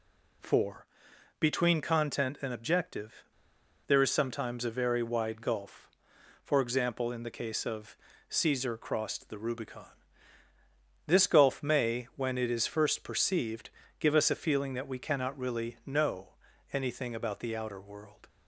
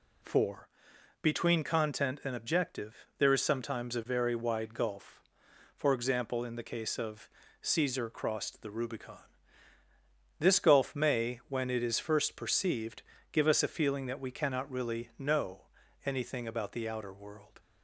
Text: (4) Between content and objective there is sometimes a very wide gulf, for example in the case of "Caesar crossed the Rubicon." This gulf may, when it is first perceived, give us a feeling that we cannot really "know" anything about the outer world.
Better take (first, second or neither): second